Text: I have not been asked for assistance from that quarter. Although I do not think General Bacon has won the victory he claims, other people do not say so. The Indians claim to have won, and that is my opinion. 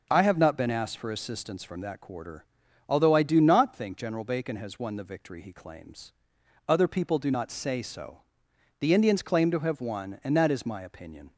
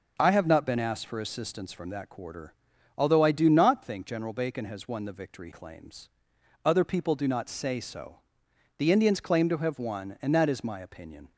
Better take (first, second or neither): first